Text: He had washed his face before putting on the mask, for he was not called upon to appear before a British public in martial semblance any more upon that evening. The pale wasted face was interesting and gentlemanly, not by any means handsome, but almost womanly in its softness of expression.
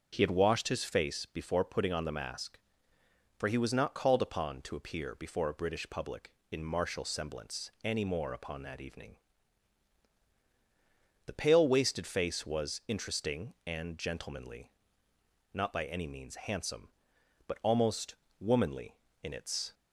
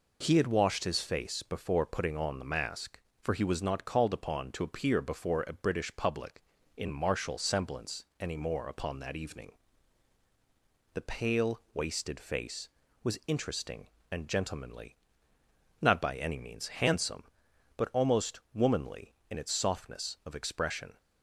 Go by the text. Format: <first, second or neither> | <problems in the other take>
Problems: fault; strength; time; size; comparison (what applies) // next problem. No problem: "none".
second | starts louder than the rest; until 1.1 s; 6.5 dB // pauses between "almost" and "womanly"; slight; at 18.1 s; 0.24 s long // stops before "softness of expression"; at 19.7 s